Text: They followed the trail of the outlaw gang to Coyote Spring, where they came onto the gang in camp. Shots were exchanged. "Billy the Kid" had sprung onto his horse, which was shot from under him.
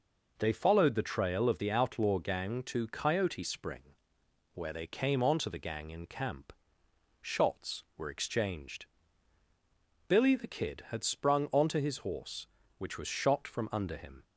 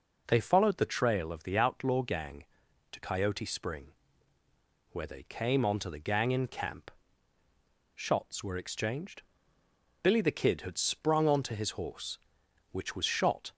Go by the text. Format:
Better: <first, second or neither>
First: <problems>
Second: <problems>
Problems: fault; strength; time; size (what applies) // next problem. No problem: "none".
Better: first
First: none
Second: stops before "from under him"; at 13.5 s